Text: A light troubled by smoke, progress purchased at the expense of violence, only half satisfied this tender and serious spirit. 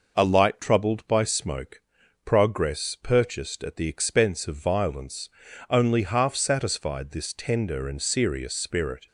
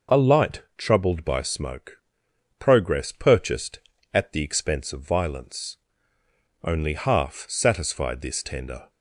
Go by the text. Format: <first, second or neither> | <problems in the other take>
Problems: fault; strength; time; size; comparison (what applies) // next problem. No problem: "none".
first | stops before "and serious spirit"; at 8.8 s